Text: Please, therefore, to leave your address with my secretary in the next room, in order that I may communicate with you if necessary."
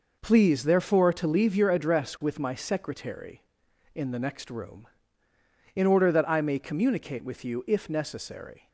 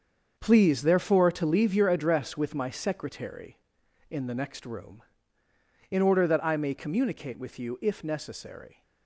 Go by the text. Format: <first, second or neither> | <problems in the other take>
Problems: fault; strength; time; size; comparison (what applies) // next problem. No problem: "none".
first | gets quieter; strong; throughout; 10.5 dB